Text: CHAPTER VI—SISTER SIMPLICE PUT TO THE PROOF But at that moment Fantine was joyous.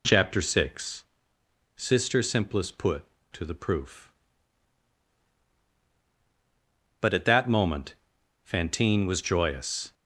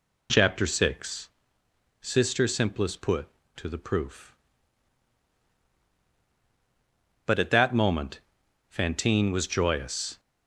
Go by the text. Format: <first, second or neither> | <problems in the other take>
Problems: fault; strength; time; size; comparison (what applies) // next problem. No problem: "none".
neither | pauses between "moment" and "Fantine"; noticeable; the same in both